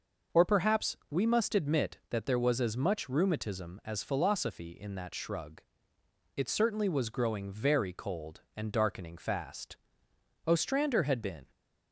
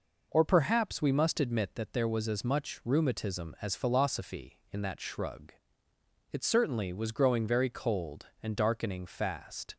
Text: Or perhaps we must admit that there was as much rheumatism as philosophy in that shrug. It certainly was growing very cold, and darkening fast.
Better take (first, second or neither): second